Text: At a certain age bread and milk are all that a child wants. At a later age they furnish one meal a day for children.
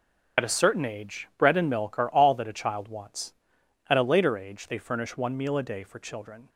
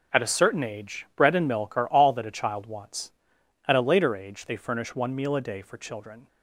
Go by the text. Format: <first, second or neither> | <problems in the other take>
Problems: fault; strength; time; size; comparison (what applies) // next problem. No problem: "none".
second | loses the start of "At"; at 0.3 s; 40 ms // starts louder than the rest; until 1.5 s; 6.5 dB; also in the second